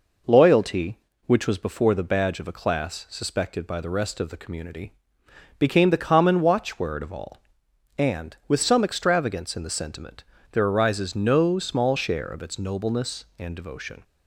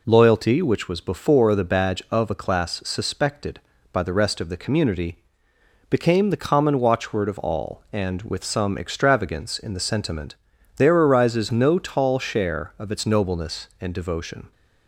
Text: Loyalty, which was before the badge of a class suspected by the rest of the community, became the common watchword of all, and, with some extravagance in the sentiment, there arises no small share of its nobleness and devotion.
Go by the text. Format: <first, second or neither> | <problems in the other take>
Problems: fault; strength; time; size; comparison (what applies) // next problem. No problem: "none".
first | says "tall" for "small"; at 11.7 s